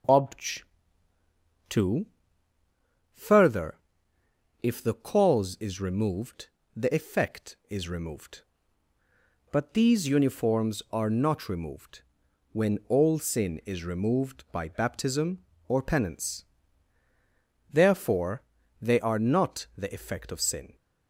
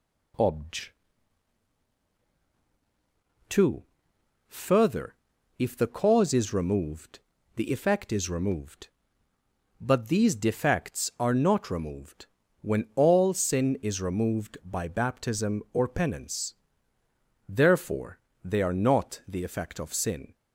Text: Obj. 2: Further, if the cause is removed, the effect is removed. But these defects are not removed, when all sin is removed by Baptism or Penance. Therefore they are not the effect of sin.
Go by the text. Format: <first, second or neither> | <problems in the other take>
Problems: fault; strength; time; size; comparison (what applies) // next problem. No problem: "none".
second | says "uniforms" for "defects"; at 10.0 s // pauses between "Therefore" and "they"; slight; at 18.4 s; 0.36 s long; slight in the second